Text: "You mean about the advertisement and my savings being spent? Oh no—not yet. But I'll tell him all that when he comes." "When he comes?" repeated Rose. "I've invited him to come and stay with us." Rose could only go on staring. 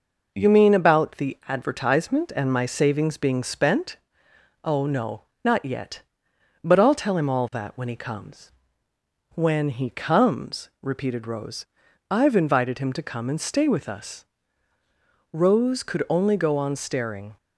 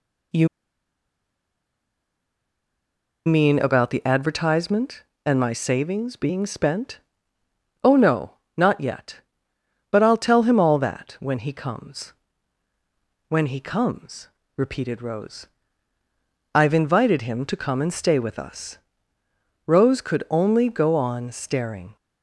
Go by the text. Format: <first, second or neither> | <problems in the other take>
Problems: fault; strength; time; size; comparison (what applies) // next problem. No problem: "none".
first | pauses between "You" and "mean"; strong; at 0.4 s; 2.7 s long